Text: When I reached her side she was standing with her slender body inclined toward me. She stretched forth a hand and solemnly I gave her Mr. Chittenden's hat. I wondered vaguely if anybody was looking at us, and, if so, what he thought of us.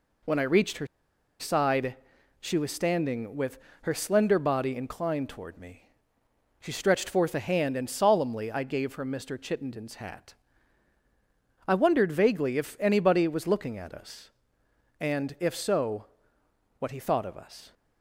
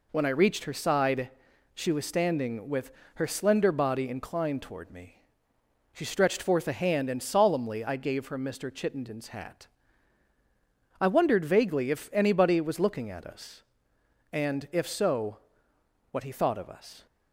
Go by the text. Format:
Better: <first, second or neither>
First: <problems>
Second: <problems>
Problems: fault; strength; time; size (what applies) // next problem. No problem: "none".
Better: second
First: pauses between "her" and "side"; noticeable; at 0.8 s; 0.53 s long // pauses between "side" and "she"; at 1.9 s; 0.44 s long // pauses between "with" and "her"; slight; at 3.5 s; 0.26 s long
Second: pauses between "side" and "she"; at 1.2 s; 0.44 s long // pauses between "with" and "her"; slight; at 2.9 s; 0.26 s long